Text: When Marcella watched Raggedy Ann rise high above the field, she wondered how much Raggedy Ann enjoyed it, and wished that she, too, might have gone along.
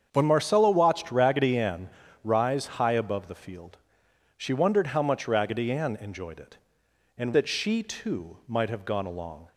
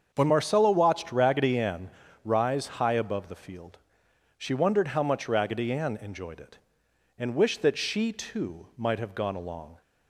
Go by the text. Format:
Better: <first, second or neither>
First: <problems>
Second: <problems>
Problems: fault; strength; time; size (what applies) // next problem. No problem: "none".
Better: second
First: starts louder than the rest; strong; until 1.1 s; 7.5 dB // pauses between "Ann" and "rise"; slight; at 1.8 s; 0.36 s long // skips "wished"; at 7.3 s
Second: starts louder than the rest; until 1.1 s; 7 dB // pauses between "Ann" and "rise"; slight; at 1.8 s; 0.36 s long